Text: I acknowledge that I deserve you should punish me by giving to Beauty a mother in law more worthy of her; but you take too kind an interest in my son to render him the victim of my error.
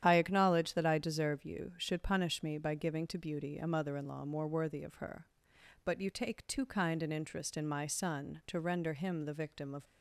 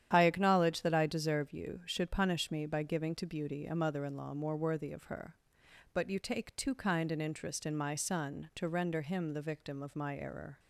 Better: second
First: starts louder than the rest; strong; until 1.0 s; 10 dB // stops before "my error"; at 9.8 s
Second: starts louder than the rest; strong; until 1.1 s; 10 dB

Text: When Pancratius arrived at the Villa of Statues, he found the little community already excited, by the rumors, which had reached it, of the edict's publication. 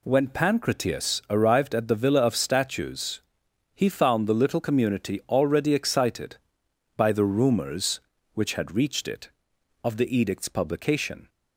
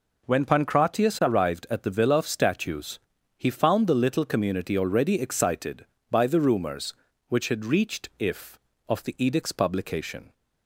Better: first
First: none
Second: says "if" for "it"; at 8.1 s

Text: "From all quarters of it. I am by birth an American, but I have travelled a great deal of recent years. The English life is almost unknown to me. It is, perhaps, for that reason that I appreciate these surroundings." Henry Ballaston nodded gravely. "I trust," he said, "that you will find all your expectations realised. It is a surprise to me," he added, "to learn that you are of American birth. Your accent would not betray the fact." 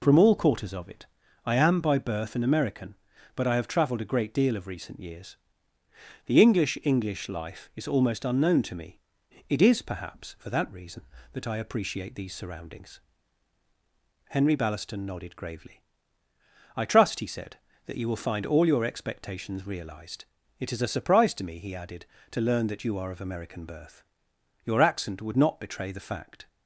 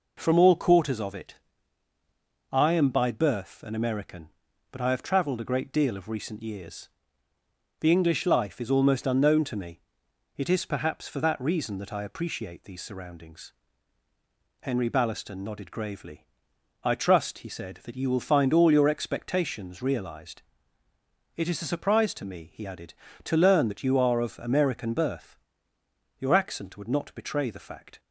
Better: second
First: says "English" twice; at 6.8 s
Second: none

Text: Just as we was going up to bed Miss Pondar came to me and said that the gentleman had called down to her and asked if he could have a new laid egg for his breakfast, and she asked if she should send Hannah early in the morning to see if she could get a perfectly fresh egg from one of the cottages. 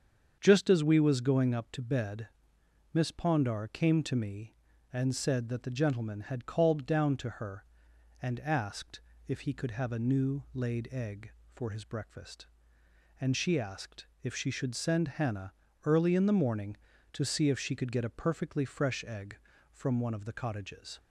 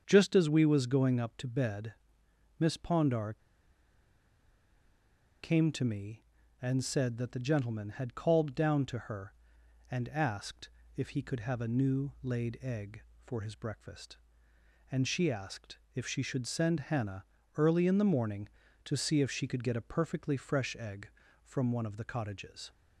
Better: first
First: starts louder than the rest; strong; until 1.4 s; 7 dB // pauses between "bed" and "Miss"; noticeable; at 2.2 s; 0.64 s long // pauses between "asked" and "if"; slight; at 9.0 s; 0.26 s long // pauses between "asked" and "if"; slight; at 14.0 s; 0.16 s long // pauses between "Hannah" and "early"; slight; at 15.5 s; 0.32 s long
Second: starts louder than the rest; strong; until 1.0 s; 7 dB // pauses between "bed" and "Miss"; noticeable; at 1.9 s; 0.64 s long // pauses between "Pondar" and "came"; strong; at 3.3 s; 2.1 s long // pauses between "asked" and "if"; slight; at 10.6 s; 0.26 s long // pauses between "asked" and "if"; slight; at 15.7 s; 0.16 s long // pauses between "Hannah" and "early"; slight; at 17.2 s; 0.32 s long

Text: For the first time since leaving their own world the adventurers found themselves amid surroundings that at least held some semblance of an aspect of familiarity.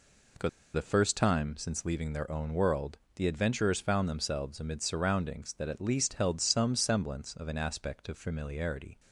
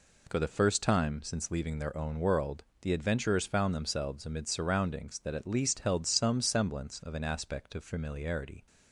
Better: second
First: pauses between "For" and "the"; slight; at 0.4 s; 0.25 s long // pauses between "world" and "the"; slight; at 2.9 s; 0.20 s long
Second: pauses between "world" and "the"; slight; at 2.6 s; 0.20 s long

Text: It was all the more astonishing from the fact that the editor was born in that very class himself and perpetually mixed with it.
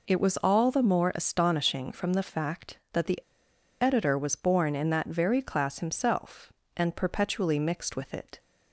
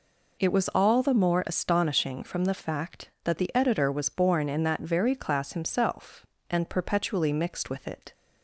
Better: second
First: pauses between "the" and "editor"; noticeable; at 3.1 s; 0.62 s long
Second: none

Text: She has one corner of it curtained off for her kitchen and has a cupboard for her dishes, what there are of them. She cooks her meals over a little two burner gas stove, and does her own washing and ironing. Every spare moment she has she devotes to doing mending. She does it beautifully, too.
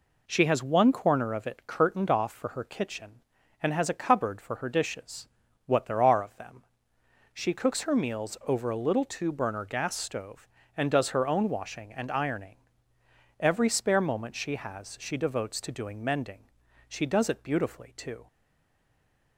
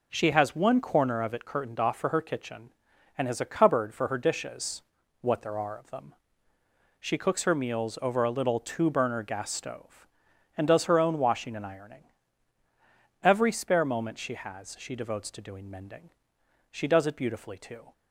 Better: second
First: stays silent after the last word; from 18.2 s on; 1.1 s long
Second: none

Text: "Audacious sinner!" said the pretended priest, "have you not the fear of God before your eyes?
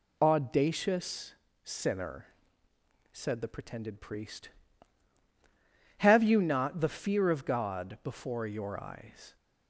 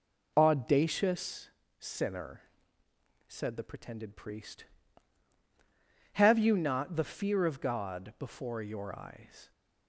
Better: first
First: pauses between "Audacious" and "sinner"; slight; at 1.3 s; 0.28 s long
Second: starts louder than the rest; noticeable; until 1.3 s; 4 dB // pauses between "Audacious" and "sinner"; slight; at 1.5 s; 0.28 s long

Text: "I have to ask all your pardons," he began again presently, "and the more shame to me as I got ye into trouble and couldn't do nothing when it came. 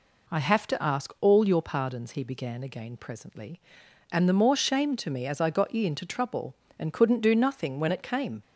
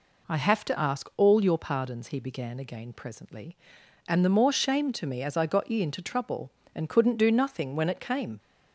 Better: neither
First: none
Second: none

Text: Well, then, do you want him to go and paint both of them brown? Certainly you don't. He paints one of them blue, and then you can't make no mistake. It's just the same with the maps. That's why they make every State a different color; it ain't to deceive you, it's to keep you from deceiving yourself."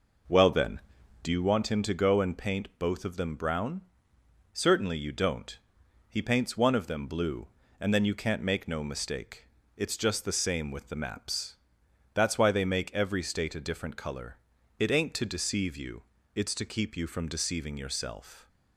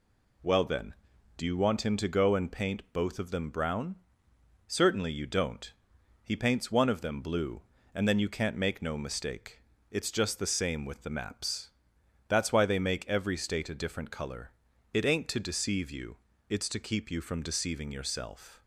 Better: second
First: starts louder than the rest; noticeable; until 1.5 s; 5 dB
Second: none

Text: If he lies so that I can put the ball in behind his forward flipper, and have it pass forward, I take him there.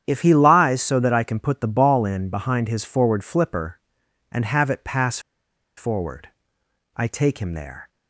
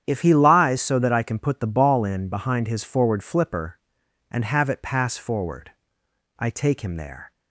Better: second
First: starts louder than the rest; strong; until 1.0 s; 9 dB // pauses between "pass" and "forward"; noticeable; at 5.1 s; 0.58 s long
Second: starts louder than the rest; strong; until 1.0 s; 9 dB

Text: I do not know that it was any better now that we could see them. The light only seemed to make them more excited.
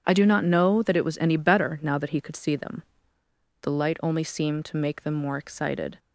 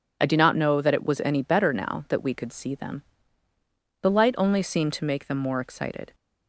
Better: second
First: starts louder than the rest; strong; until 1.0 s; 8 dB // says "he" for "we"; at 2.1 s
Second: none

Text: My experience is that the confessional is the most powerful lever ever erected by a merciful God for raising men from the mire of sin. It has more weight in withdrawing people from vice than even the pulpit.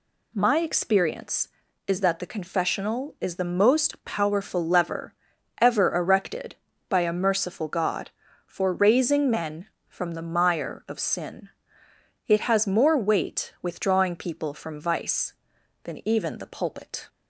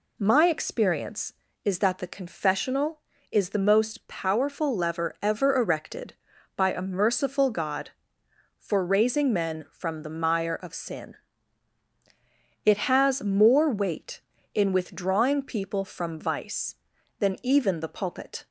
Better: second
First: pauses between "lever" and "ever"; noticeable; at 5.1 s; 0.48 s long // skips "in"; at 13.5 s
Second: none

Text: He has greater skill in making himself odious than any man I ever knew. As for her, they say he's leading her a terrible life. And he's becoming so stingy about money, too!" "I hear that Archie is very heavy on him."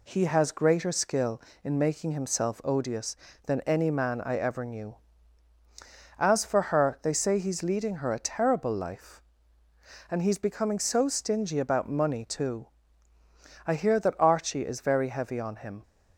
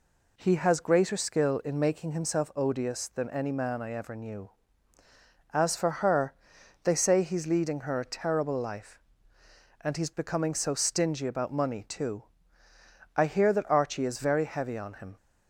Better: neither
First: none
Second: none

